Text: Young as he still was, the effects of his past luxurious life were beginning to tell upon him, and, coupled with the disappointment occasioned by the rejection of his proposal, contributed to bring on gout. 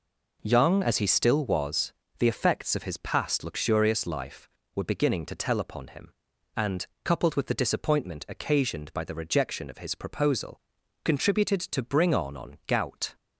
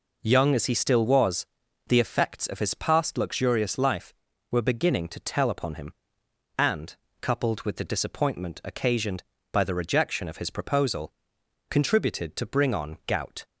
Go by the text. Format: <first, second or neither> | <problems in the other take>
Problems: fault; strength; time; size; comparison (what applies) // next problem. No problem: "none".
second | says "on" twice; at 12.3 s